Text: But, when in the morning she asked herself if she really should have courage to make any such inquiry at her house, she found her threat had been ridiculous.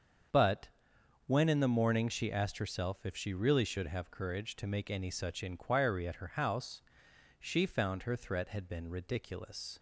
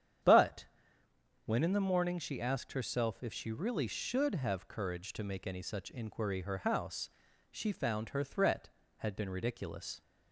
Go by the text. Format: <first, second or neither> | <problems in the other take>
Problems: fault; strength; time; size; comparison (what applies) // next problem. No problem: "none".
first | starts louder than the rest; strong; until 2.0 s; 9 dB; strong in the first // skips "at"; at 6.4 s